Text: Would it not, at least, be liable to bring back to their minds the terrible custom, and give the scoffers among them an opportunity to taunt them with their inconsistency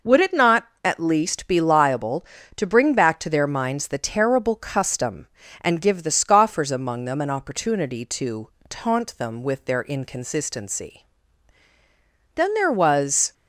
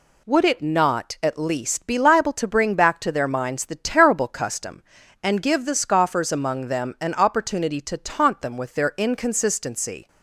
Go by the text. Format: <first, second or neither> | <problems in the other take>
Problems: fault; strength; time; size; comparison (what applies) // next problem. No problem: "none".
second | pauses between "to" and "taunt"; slight; at 8.4 s; 0.20 s long // goes on to say "Then there was"; noticeable; from 12.3 s on; 0.98 s long